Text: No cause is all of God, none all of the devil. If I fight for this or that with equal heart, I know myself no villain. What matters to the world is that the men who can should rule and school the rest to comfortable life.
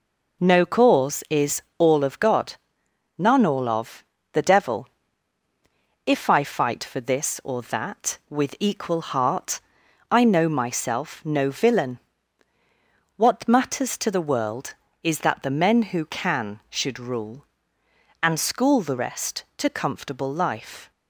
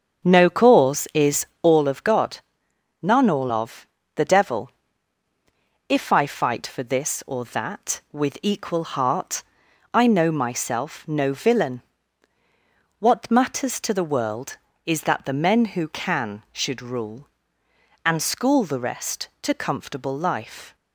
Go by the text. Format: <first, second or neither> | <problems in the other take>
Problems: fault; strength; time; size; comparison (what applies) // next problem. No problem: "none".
first | starts louder than the rest; strong; until 1.8 s; 7.5 dB // pauses between "is" and "all"; slight; at 1.4 s; 0.16 s long; slight in the first // pauses between "of" and "the"; slight; at 3.8 s; 0.30 s long; slight in the first